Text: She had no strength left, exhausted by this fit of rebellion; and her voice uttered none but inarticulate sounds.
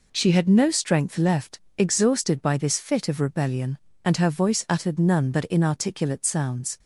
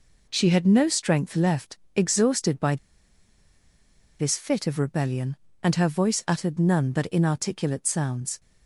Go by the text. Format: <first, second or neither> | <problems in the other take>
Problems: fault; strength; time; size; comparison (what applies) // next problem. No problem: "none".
first | pauses between "by" and "this"; strong; at 2.7 s; 1.4 s long